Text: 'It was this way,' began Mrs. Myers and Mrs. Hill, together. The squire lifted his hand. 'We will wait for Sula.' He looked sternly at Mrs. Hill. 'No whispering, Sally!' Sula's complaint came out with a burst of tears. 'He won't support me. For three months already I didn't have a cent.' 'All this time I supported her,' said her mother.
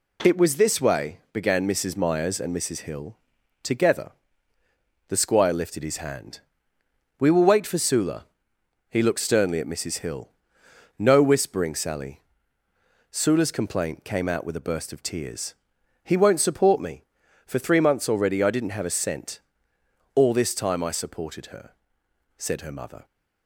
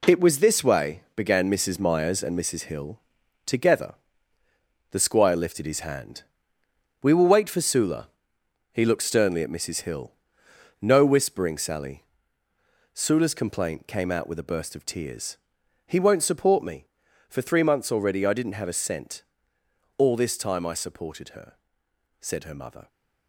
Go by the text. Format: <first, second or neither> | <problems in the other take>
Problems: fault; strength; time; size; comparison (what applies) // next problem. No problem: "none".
first | gets quieter; strong; throughout; 8.5 dB